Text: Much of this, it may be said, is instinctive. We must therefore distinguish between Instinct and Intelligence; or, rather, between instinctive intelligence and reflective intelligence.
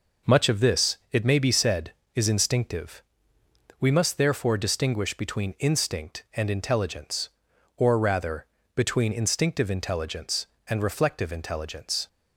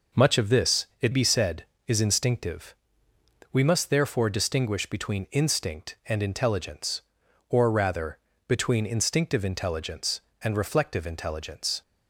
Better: first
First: none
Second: skips "may"; at 1.1 s

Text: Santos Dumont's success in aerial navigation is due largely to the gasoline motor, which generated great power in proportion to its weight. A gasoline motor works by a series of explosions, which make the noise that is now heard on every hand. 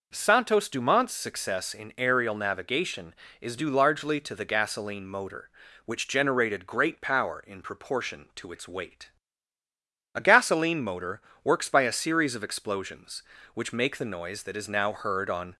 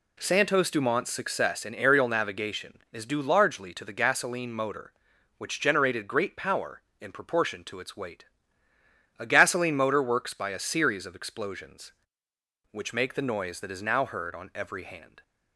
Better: second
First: pauses between "motor" and "works"; slight; at 11.2 s; 0.22 s long // stops before "every hand"; at 15.5 s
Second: none

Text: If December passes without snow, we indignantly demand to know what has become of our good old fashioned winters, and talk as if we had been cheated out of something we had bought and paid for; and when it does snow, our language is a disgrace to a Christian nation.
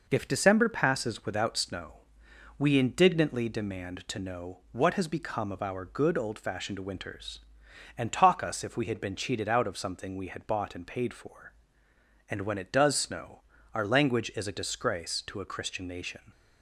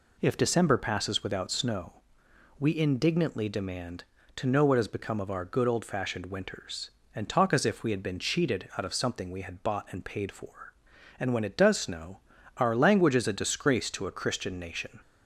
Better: second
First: says "us" for "as"; at 8.4 s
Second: none

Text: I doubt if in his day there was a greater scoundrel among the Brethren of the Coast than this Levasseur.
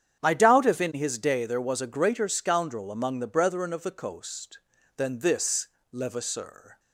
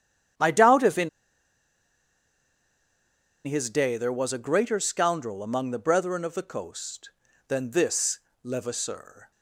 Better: first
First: starts louder than the rest; strong; until 1.2 s; 9 dB // pauses between "this" and "Levasseur"; slight; at 5.6 s; 0.26 s long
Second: starts louder than the rest; strong; until 3.7 s; 9 dB // pauses between "in" and "his"; strong; at 1.0 s; 2.3 s long // pauses between "this" and "Levasseur"; slight; at 8.1 s; 0.26 s long

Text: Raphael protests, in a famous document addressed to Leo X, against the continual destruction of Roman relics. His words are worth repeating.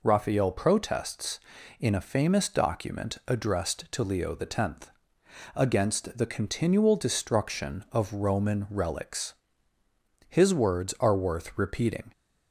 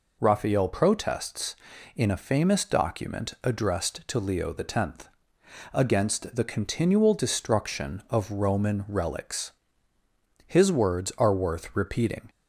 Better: neither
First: none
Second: none

